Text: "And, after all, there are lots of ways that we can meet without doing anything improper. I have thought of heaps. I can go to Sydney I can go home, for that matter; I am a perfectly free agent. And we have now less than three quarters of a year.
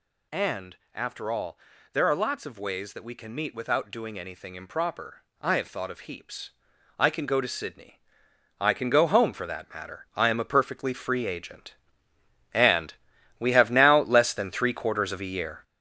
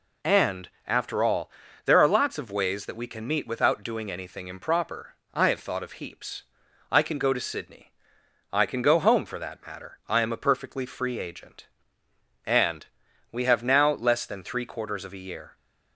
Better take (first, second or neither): second